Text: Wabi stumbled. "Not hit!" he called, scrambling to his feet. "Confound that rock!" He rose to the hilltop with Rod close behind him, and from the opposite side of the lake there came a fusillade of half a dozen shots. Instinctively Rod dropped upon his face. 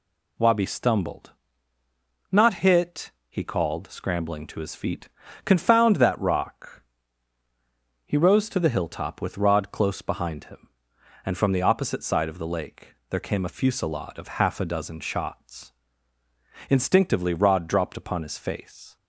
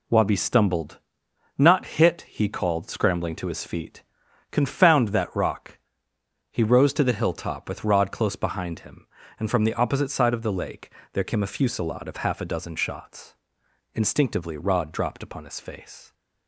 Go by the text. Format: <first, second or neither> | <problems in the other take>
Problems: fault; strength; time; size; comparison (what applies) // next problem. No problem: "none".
neither | pauses between "lake" and "there"; slight; the same in both